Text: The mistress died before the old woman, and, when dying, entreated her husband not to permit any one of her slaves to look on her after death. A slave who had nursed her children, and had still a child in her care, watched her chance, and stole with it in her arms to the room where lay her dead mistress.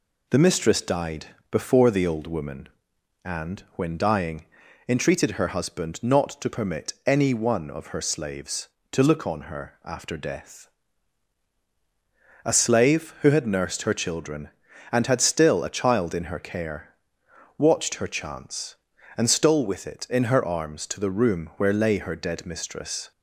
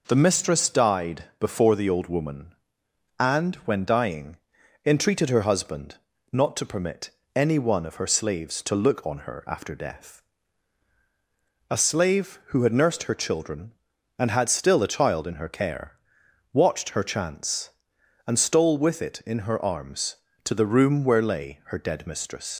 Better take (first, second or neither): first